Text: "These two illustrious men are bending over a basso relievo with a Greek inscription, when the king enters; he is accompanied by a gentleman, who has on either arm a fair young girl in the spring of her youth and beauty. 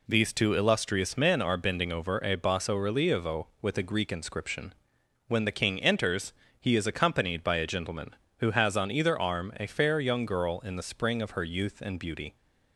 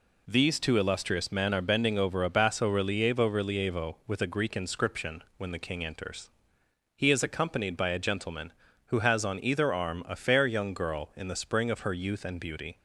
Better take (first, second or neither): first